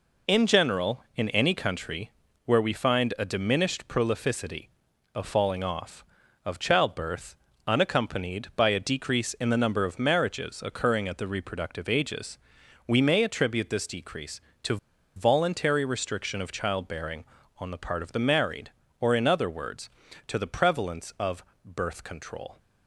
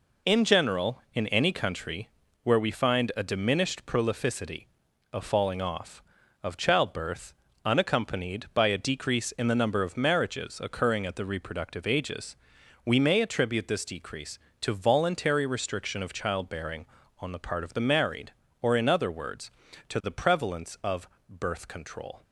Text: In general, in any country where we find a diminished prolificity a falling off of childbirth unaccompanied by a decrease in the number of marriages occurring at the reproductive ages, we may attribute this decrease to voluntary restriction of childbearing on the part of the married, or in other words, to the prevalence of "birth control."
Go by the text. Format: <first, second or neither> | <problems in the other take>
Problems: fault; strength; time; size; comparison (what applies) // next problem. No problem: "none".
second | pauses between "country" and "where"; slight; at 2.1 s; 0.32 s long; slight in the second // pauses between "prolificity" and "a"; noticeable; at 4.6 s; 0.48 s long; noticeable in the second // pauses between "childbirth" and "unaccompanied"; slight; at 7.3 s; 0.32 s long; slight in the second // pauses between "to" and "voluntary"; at 14.7 s; 0.39 s long // pauses between "of" and "birth"; slight; at 21.4 s; 0.18 s long; slight in the second